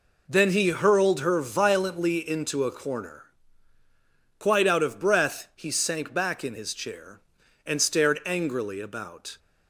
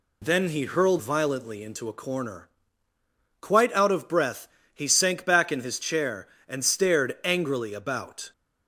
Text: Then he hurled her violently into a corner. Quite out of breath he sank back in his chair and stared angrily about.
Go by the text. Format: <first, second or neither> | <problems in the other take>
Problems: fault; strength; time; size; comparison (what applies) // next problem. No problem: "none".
first | skips "her"; at 0.9 s // pauses between "breath" and "he"; slight; at 4.4 s; 0.26 s long